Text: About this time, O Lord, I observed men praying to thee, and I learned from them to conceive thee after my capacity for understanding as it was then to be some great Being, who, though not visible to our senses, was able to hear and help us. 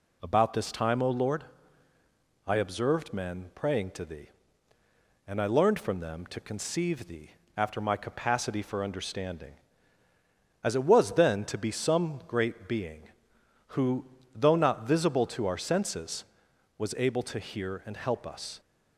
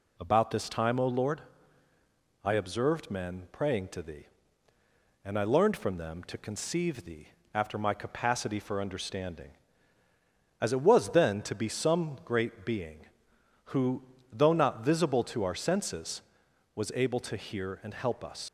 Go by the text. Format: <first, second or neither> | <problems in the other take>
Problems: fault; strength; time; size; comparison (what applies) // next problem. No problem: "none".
first | pauses between "thee" and "after"; slight; at 7.2 s; 0.26 s long; slight in the first // leaves "us" unfinished; at 18.4 s; 85 ms